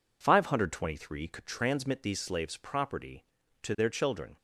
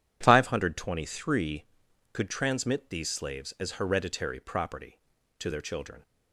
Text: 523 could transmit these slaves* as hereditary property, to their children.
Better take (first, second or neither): second